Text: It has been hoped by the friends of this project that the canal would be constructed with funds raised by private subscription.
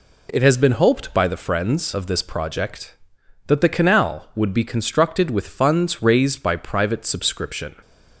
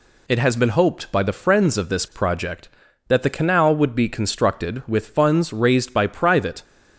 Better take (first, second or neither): first